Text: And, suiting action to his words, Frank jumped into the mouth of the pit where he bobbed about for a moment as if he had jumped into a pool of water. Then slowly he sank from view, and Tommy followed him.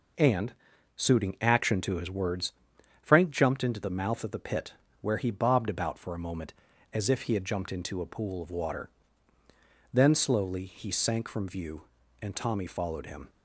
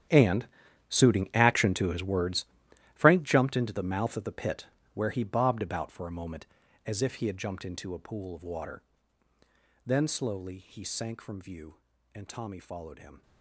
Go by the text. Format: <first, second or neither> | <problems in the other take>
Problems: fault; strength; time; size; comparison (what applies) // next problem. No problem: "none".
first | gets quieter; strong; throughout; 16 dB // pauses between "pit" and "where"; slight; at 4.6 s; 0.28 s long; slight in the first